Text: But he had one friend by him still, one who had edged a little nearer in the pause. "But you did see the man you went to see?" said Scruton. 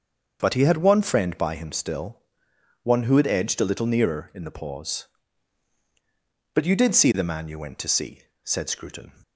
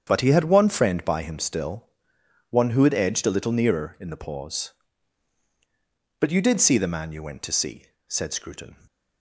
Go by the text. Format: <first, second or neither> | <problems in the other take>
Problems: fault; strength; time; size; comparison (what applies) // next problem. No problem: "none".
first | gets quieter; strong; throughout; 10 dB // starts louder than the rest; strong; until 1.0 s; 8 dB; also in the first